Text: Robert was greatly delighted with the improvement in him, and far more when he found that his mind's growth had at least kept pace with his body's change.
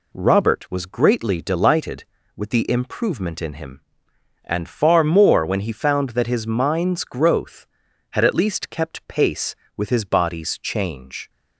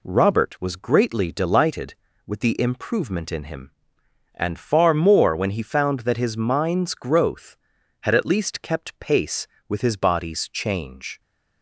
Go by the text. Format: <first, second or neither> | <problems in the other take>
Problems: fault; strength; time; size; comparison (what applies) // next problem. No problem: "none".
neither | none